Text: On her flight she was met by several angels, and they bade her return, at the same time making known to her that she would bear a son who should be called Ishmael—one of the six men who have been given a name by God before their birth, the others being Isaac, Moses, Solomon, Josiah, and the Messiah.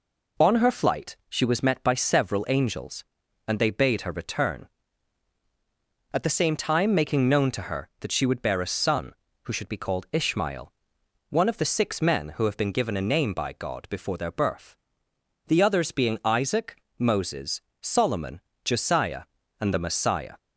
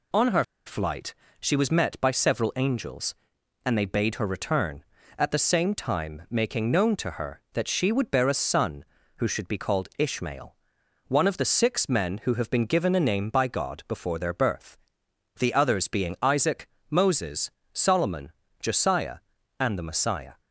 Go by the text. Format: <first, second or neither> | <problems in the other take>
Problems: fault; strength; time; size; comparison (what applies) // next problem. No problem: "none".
first | pauses between "her" and "flight"; slight; at 0.4 s; 0.22 s long // pauses between "flight" and "she"; slight; at 1.1 s; 0.28 s long